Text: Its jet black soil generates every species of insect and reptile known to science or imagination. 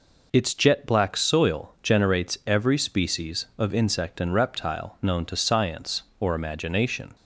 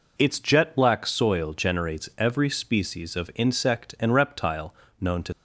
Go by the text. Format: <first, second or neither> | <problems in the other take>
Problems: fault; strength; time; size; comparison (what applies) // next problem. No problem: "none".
first | pauses between "reptile" and "known"; slight; at 4.7 s; 0.26 s long // stops before "science or imagination"; at 5.3 s